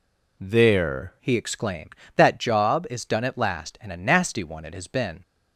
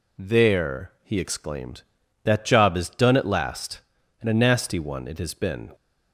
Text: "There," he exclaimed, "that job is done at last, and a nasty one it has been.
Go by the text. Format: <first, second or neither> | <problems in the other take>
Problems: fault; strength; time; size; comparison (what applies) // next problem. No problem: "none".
second | changes voice at "he"; from 1.1 s on; 4.1 s long